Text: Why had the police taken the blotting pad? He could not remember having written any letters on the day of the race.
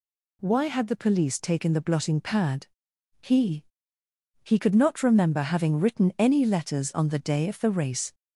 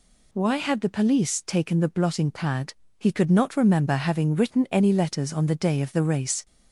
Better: second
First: says "He" twice; at 4.4 s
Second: none

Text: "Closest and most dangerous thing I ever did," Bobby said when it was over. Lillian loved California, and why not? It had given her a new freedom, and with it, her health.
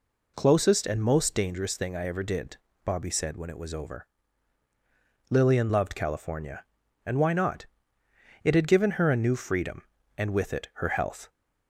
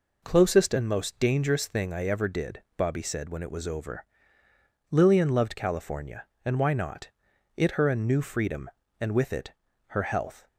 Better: first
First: none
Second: skips "had given"; at 7.7 s

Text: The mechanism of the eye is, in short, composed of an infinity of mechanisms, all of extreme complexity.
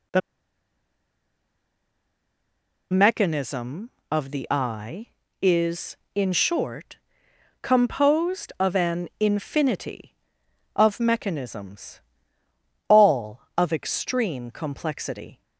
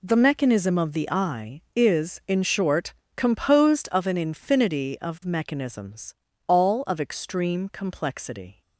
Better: second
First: pauses between "The" and "mechanism"; strong; at 0.2 s; 2.7 s long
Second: none

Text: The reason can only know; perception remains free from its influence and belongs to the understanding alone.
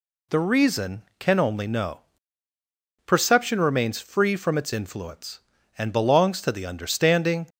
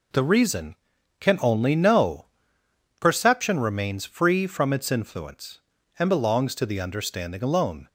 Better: second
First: stops before "alone"; at 7.4 s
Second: none

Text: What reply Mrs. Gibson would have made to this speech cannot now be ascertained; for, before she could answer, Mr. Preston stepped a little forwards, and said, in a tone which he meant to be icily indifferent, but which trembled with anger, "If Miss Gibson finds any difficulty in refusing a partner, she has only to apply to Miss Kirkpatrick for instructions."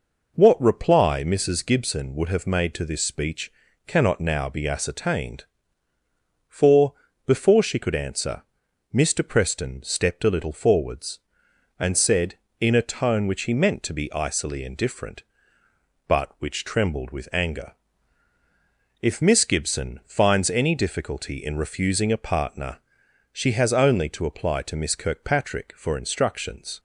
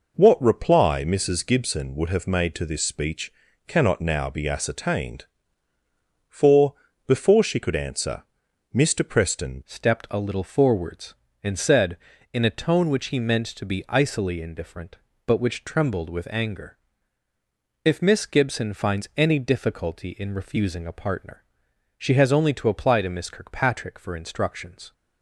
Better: first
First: pauses between "speech" and "cannot"; slight; at 3.5 s; 0.34 s long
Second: pauses between "speech" and "cannot"; slight; at 3.3 s; 0.34 s long // changes voice at "stepped"; from 9.6 s on; 15.3 s long

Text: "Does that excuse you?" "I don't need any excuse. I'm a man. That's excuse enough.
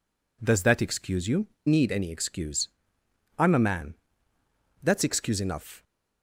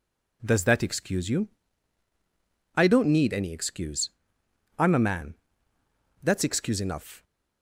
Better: second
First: skips "I don't"; at 1.5 s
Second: none

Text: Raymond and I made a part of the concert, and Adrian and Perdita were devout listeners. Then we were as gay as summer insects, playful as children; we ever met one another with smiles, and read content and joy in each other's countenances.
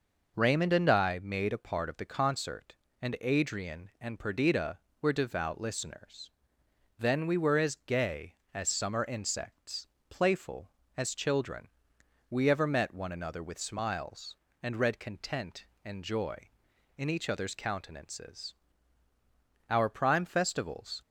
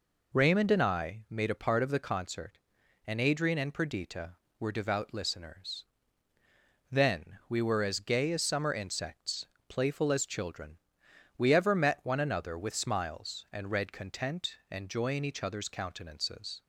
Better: second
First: goes on to say "Our prime festivals"; from 19.6 s on; 1.3 s long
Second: none

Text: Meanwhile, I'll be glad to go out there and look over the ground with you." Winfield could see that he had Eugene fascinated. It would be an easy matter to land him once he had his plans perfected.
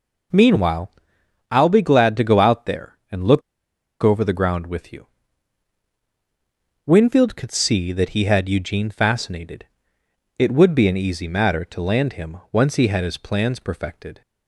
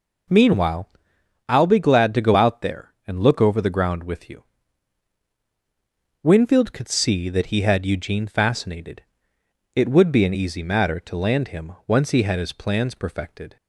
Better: second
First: pauses between "look" and "over"; noticeable; at 3.4 s; 0.61 s long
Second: none

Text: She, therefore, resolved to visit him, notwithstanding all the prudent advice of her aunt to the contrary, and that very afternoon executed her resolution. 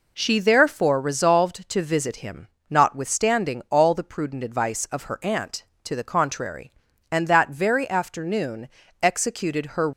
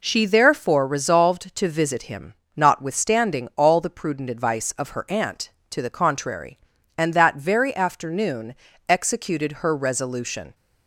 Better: second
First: pauses between "afternoon" and "executed"; slight; at 8.6 s; 0.34 s long // stops before "resolution"; at 9.9 s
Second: pauses between "afternoon" and "executed"; slight; at 8.5 s; 0.34 s long

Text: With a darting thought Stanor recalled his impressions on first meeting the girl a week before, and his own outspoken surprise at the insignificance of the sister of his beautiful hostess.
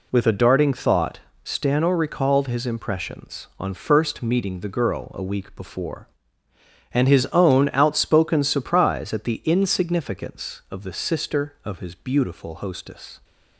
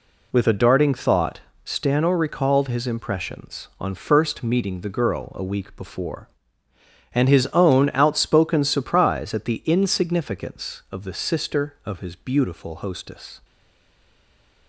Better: first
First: pauses between "thought" and "Stanor"; slight; at 1.1 s; 0.24 s long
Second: pauses between "thought" and "Stanor"; slight; at 1.4 s; 0.24 s long // stays silent after the last word; noticeable; from 13.4 s on; 1.2 s long

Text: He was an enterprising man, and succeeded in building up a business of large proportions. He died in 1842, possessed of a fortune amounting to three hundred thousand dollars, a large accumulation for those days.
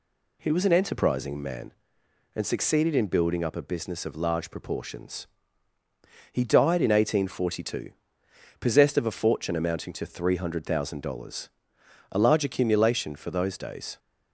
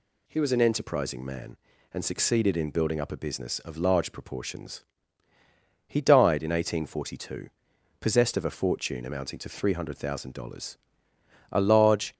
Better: first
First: none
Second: stops before "accumulation for those days"; at 12.1 s

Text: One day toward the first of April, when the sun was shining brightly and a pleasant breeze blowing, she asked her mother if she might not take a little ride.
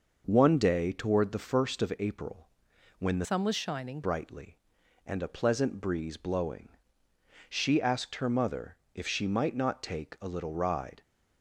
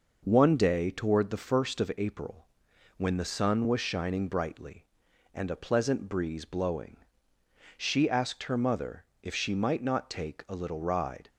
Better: second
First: changes voice from "sun" to "shining"; from 3.2 to 4.0 s; 0.8 s long // pauses between "mother" and "if"; slight; at 8.7 s; 0.18 s long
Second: pauses between "mother" and "if"; slight; at 9.0 s; 0.18 s long

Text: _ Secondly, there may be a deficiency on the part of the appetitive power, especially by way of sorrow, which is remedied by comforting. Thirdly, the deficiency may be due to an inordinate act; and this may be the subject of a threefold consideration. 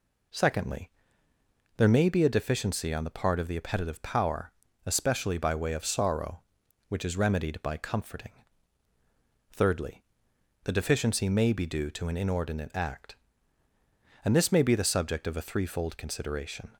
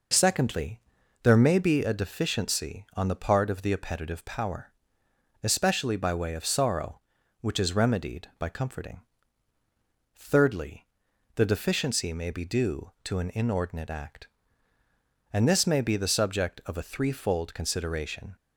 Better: neither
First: none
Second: none

